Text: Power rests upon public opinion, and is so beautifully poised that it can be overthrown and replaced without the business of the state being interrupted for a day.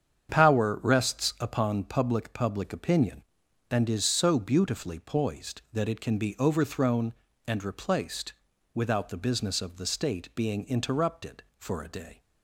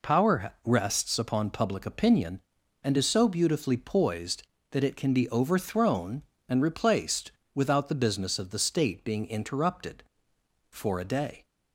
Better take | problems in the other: second | starts louder than the rest; strong; until 1.4 s; 8 dB // says "public" twice; at 2.3 s // pauses between "replaced" and "without"; at 8.3 s; 0.40 s long; slight in the second

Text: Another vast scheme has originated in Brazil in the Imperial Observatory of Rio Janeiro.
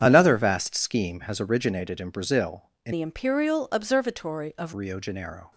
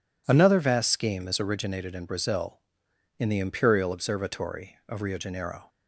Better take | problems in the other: second | starts louder than the rest; strong; until 1.0 s; 8.5 dB // changes voice from "the" to "of"; from 2.9 to 4.7 s; 1.8 s long

